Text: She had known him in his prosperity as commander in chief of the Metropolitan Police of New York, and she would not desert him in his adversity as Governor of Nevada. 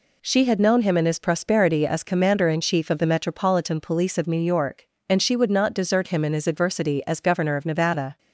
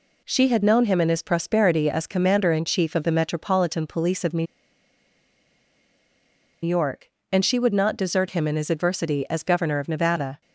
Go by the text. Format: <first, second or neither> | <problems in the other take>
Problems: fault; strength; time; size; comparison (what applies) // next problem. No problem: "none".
first | pauses between "New" and "York"; strong; at 4.4 s; 2.1 s long